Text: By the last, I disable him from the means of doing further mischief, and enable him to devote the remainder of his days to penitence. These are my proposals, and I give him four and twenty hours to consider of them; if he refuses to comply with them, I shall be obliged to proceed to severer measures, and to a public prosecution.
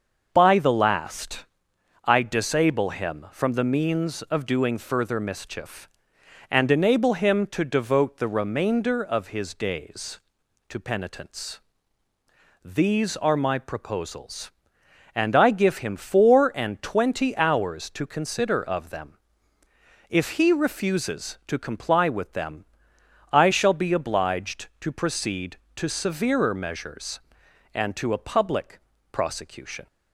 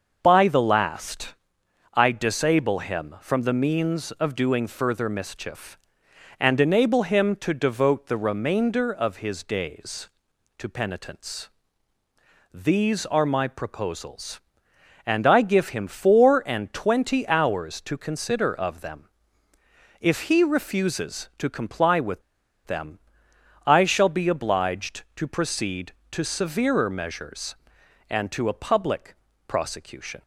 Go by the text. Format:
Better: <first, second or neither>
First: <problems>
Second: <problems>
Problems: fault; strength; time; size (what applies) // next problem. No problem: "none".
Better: first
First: starts louder than the rest; until 1.3 s; 6.5 dB // pauses between "public" and "prosecution"; slight; at 28.8 s; 0.32 s long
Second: starts louder than the rest; until 1.2 s; 6.5 dB // pauses between "with" and "them"; at 22.2 s; 0.45 s long // pauses between "public" and "prosecution"; slight; at 29.1 s; 0.32 s long